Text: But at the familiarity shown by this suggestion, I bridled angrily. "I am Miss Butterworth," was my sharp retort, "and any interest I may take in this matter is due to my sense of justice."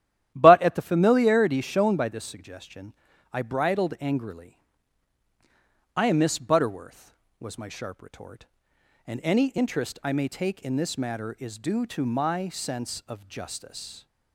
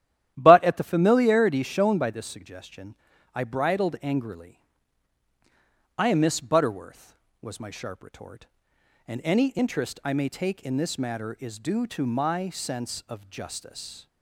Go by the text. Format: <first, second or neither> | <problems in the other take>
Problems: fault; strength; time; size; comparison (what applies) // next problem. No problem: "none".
neither | starts louder than the rest; strong; the same in both